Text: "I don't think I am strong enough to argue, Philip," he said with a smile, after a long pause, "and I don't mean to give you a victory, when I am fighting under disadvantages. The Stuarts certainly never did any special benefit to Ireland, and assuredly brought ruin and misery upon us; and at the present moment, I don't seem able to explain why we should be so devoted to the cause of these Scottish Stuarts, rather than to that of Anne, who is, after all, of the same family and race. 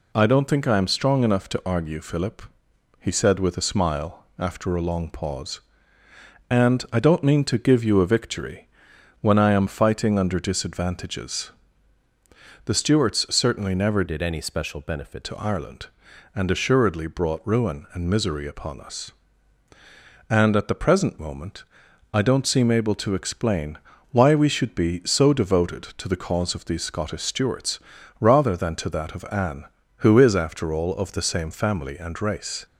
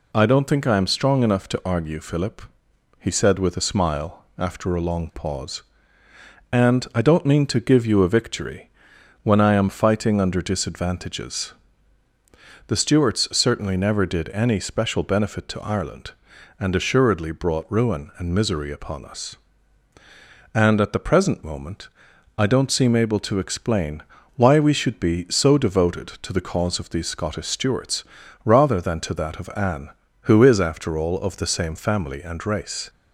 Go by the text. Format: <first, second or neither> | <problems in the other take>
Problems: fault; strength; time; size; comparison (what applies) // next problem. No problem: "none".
second | changes voice from "did" to "benefit"; from 14.0 to 15.2 s; 1.2 s long // pauses between "explain" and "why"; slight; at 23.7 s; 0.36 s long; slight in the second